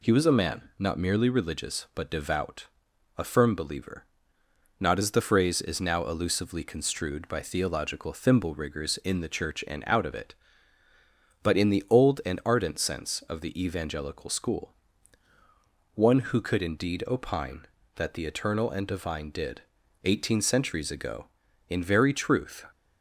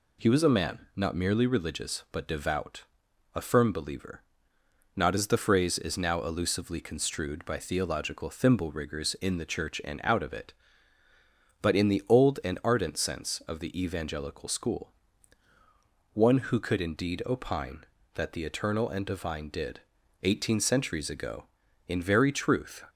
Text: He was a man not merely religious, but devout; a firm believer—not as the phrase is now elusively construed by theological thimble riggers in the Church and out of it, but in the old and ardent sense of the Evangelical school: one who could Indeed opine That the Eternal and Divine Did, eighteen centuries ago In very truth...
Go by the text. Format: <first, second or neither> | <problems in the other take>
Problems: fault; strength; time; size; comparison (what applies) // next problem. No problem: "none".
neither | none